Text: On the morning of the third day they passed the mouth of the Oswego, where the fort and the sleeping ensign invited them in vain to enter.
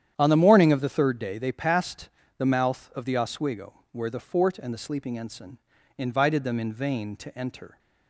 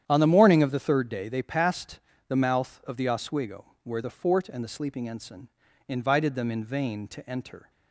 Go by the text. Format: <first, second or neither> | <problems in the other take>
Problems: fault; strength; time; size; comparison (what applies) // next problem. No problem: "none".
neither | starts louder than the rest; strong; the same in both // pauses between "passed" and "the"; slight; the same in both // pauses between "ensign" and "invited"; the same in both